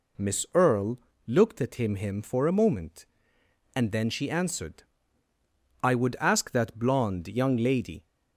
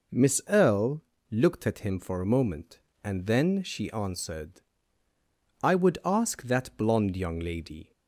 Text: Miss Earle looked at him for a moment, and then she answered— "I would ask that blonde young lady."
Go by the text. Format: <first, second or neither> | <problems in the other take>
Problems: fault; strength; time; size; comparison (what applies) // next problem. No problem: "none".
second | pauses between "Earle" and "looked"; slight; at 0.9 s; 0.30 s long; slight in the second // says "him" twice; at 1.9 s